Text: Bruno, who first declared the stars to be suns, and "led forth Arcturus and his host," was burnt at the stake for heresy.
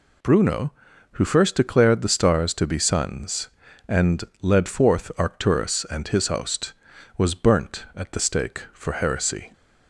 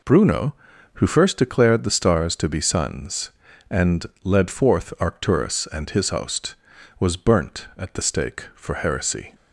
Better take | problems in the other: first | starts louder than the rest; noticeable; until 1.4 s; 4 dB // pauses between "and" and "led"; slight; at 4.0 s; 0.20 s long; slight in the first

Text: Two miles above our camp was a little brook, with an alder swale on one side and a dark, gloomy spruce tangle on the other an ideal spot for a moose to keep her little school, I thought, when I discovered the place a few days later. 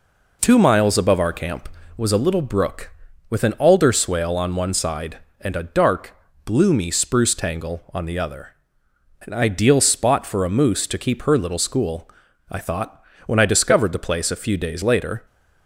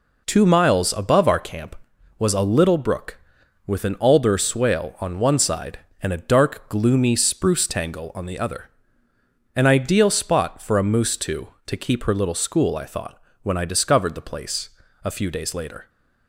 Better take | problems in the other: first | pauses between "other" and "an"; noticeable; at 8.6 s; 0.86 s long; noticeable in the first // says "to" twice; at 11.6 s // pauses between "place" and "a"; slight; at 14.6 s; 0.34 s long

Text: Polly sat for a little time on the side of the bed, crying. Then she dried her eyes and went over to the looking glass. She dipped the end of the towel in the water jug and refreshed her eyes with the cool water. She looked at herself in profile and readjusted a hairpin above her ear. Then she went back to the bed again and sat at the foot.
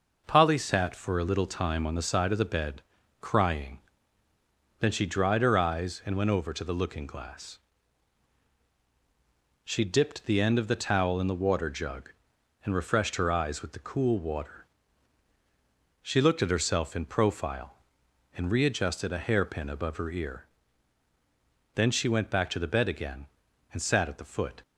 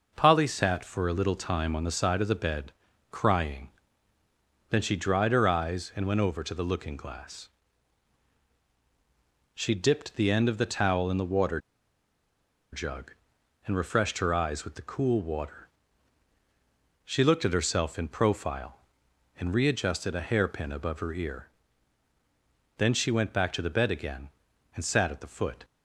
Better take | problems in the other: first | pauses between "water" and "jug"; at 11.5 s; 1.1 s long

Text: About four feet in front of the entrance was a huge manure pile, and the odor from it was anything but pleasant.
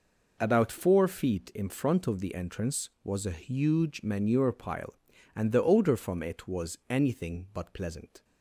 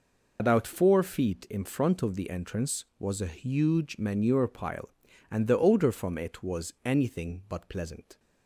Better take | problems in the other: first | loses the start of "About"; at 0.3 s; 45 ms

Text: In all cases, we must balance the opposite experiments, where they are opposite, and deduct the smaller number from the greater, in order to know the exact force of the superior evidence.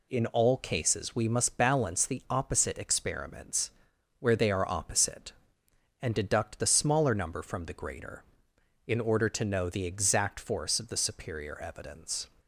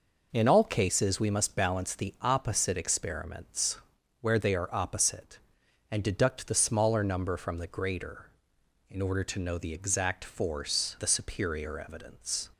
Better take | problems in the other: first | skips "of"; at 10.9 s

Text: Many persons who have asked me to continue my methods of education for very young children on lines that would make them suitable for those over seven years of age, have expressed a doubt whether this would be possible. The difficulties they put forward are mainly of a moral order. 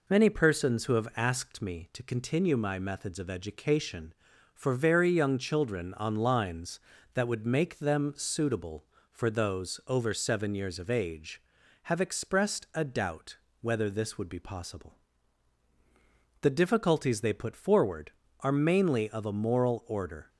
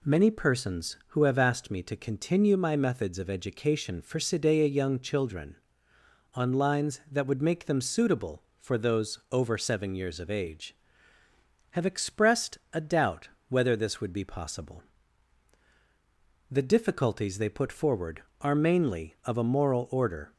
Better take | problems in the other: first | says "sidea" for "very"; at 4.1 s // pauses between "expressed" and "a"; slight; at 12.5 s; 0.16 s long // pauses between "doubt" and "whether"; slight; at 13.2 s; 0.20 s long; slight in the first

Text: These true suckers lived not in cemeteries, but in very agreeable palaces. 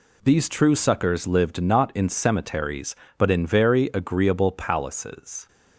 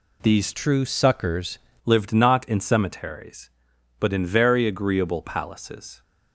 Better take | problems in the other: first | changes voice from "true" to "suckers"; from 0.5 to 1.5 s; 1.0 s long

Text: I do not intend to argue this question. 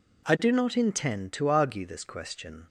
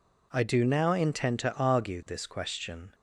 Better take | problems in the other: first | says "now" for "not"; at 0.6 s

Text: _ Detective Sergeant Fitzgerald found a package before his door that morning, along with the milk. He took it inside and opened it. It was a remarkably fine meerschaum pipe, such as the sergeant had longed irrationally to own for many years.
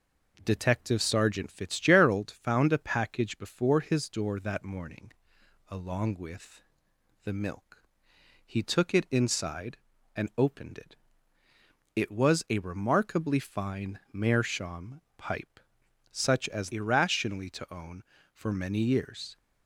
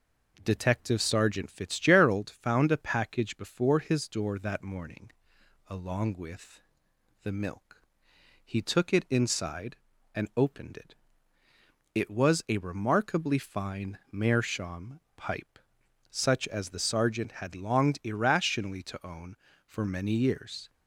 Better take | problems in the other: second | pauses between "with" and "the"; noticeable; at 6.6 s; 0.62 s long; noticeable in the second // pauses between "meerschaum" and "pipe"; slight; at 15.0 s; 0.16 s long; slight in the second // skips "the sergeant had longed"; at 16.7 s

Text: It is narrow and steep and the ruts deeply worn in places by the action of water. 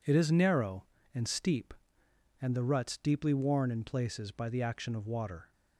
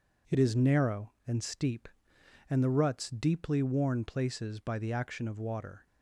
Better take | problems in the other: first | skips "in"; at 4.0 s

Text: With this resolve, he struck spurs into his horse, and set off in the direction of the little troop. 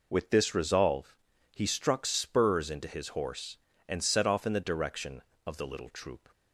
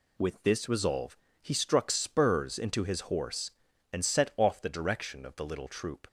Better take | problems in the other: first | skips "in"; at 4.6 s

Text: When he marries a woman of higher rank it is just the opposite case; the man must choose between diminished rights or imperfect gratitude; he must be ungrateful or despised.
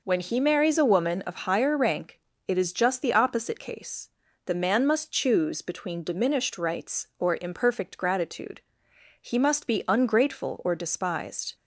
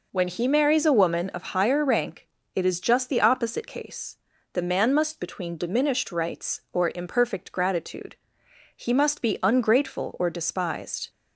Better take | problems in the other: first | pauses between "rank" and "it"; slight; at 2.2 s; 0.28 s long; slight in the first // skips "choose"; at 5.1 s

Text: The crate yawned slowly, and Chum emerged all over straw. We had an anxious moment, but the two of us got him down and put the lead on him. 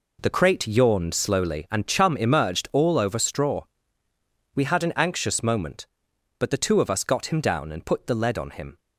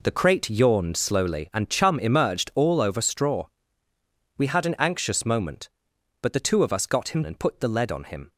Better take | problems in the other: first | skips "down"; at 7.2 s

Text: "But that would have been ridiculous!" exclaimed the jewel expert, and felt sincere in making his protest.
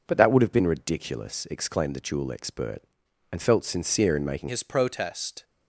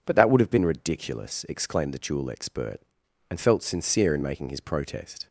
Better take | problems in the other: second | changes voice at "his"; from 4.4 s on; 1.0 s long

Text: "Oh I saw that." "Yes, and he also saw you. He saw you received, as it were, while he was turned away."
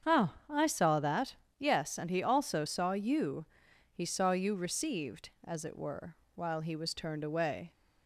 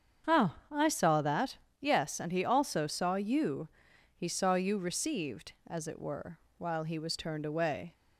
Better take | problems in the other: neither | starts louder than the rest; strong; the same in both // pauses between "Oh" and "I"; slight; the same in both

